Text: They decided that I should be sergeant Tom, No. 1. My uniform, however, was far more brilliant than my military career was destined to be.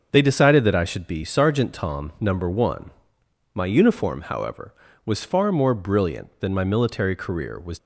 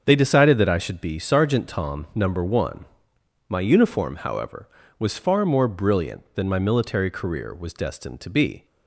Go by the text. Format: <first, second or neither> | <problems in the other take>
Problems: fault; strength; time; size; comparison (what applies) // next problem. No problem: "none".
second | starts louder than the rest; until 1.1 s; 6.5 dB; also in the second // stops before "destined to be"; at 7.7 s